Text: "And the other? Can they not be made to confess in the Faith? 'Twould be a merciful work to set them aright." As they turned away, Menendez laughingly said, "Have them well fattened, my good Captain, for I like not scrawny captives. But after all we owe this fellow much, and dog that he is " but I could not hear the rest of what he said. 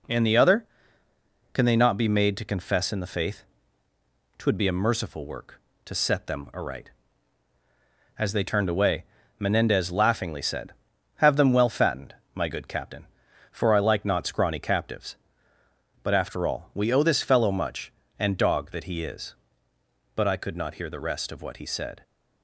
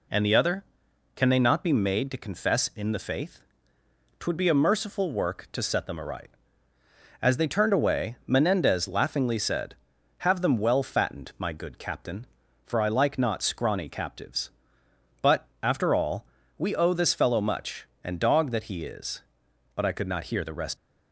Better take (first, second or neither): first